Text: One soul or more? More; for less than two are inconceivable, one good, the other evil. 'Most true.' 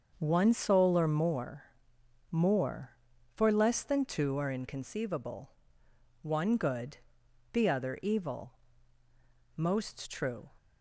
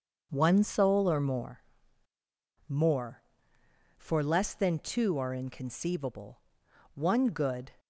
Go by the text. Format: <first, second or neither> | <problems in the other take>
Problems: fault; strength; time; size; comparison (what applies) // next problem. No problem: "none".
first | starts louder than the rest; until 1.3 s; 6.5 dB; also in the first // stops before "the other evil Most true"; at 7.7 s